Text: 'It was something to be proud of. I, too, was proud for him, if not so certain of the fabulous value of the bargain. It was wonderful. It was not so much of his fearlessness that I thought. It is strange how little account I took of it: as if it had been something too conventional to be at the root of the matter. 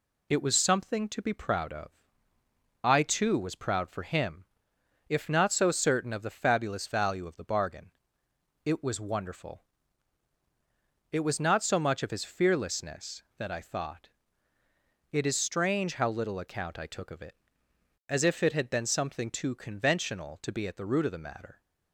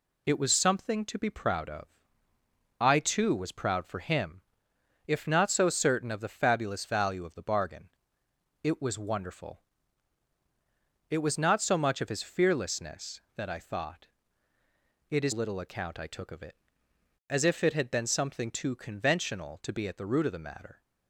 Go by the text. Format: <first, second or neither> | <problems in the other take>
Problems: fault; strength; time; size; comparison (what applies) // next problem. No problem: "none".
first | skips "strange how"; at 15.3 s